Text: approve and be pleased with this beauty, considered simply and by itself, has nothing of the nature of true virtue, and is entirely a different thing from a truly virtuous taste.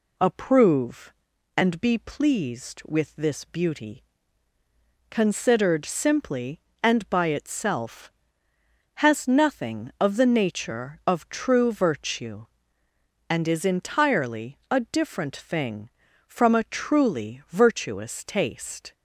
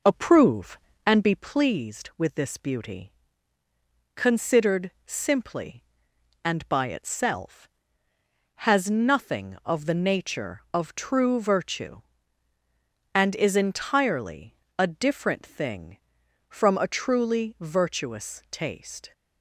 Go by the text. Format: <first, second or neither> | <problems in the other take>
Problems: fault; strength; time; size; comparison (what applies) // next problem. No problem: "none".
first | starts louder than the rest; noticeable; until 1.5 s; 5 dB // pauses between "entirely" and "a"; slight; at 14.5 s; 0.24 s long